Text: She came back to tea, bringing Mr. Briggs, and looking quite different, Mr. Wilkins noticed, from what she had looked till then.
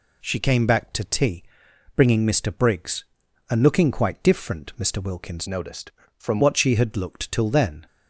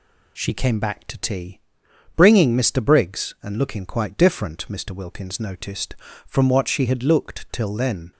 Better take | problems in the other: second | changes voice from "noticed" to "from"; from 5.4 to 6.4 s; 1.0 s long

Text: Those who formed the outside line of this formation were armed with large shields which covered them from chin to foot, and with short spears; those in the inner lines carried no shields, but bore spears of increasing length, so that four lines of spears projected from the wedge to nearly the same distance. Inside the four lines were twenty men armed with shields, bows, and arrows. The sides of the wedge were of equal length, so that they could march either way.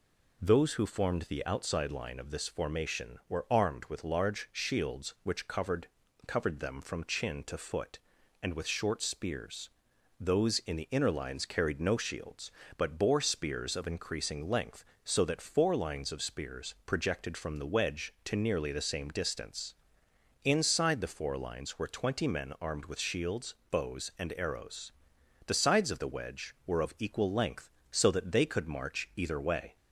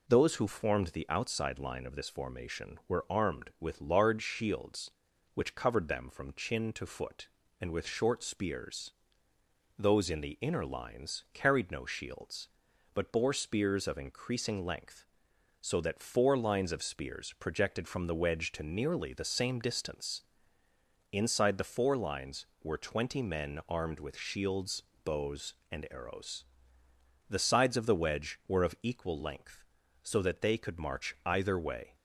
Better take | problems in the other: second | says "covered" twice; at 6.2 s

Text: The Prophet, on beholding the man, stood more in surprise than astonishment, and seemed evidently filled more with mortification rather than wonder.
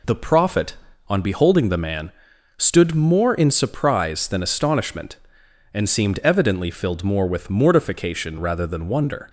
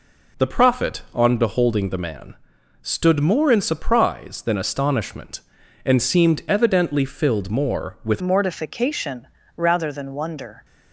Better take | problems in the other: first | changes voice at "mortification"; from 8.1 s on; 2.5 s long // pauses between "mortification" and "rather"; slight; at 9.2 s; 0.26 s long

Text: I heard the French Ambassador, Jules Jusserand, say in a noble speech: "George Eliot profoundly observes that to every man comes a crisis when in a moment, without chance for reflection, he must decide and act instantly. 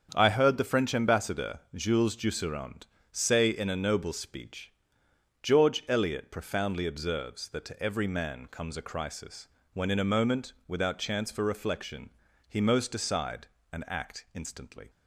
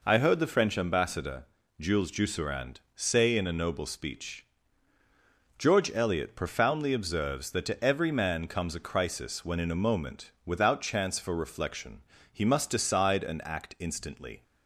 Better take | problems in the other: second | starts louder than the rest; strong; until 1.1 s; 7.5 dB // pauses between "crisis" and "when"; slight; at 9.4 s; 0.28 s long // says "most" for "must"; at 12.5 s

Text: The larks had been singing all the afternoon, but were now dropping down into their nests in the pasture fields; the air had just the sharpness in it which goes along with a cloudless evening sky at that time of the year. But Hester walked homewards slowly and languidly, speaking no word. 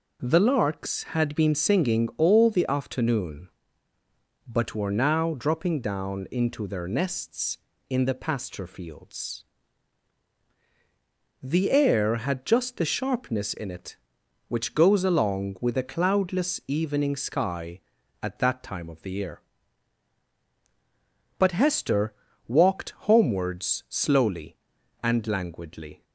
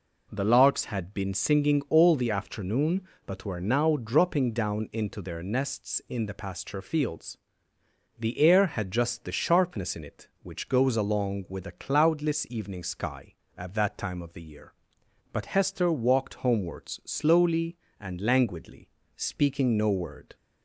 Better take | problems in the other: second | pauses between "Hester" and "walked"; slight; at 22.1 s; 0.34 s long // pauses between "walked" and "homewards"; slight; at 22.8 s; 0.16 s long // stops before "speaking no word"; at 26.0 s

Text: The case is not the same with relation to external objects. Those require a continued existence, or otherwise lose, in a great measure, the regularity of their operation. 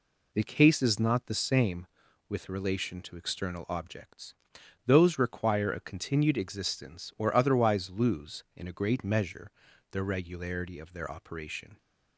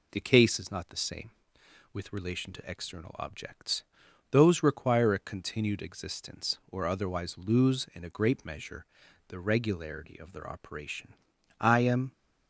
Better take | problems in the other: first | goes on to say "I am"; from 11.5 s on; 0.52 s long

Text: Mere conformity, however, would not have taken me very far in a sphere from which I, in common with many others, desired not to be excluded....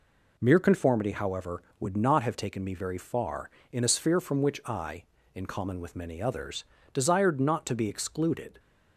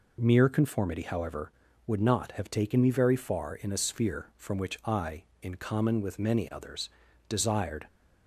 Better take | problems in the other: first | stops before "not to be excluded"; at 7.8 s

